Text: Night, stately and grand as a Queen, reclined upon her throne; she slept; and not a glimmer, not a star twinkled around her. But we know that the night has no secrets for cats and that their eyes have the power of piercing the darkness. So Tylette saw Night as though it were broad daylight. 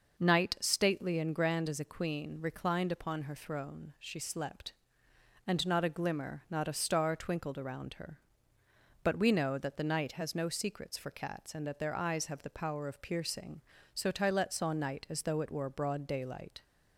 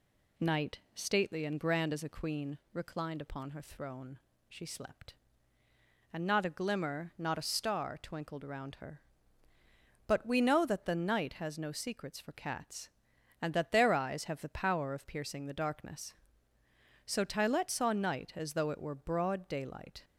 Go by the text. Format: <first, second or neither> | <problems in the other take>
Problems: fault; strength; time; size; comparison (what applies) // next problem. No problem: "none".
second | skips "the darkness"; at 13.7 s